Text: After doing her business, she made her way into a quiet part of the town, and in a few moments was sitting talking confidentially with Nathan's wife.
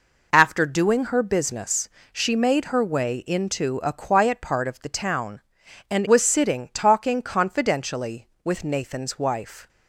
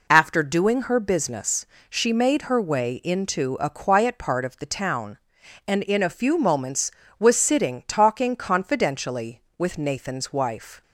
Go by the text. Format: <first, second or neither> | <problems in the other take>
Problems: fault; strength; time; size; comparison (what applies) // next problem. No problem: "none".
second | skips "in a few moments"; at 6.0 s